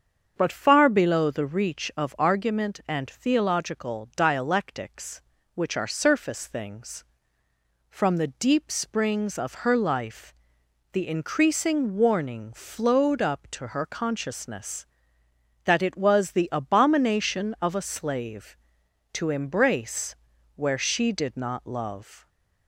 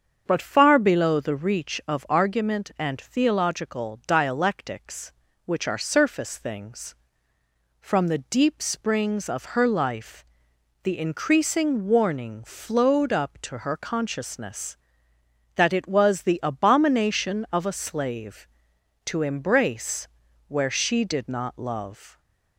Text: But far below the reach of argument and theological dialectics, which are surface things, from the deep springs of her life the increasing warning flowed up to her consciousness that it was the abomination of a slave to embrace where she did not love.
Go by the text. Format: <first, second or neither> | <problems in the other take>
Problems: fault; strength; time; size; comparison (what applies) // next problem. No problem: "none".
neither | starts louder than the rest; the same in both // pauses between "life" and "the"; noticeable; the same in both // pauses between "embrace" and "where"; the same in both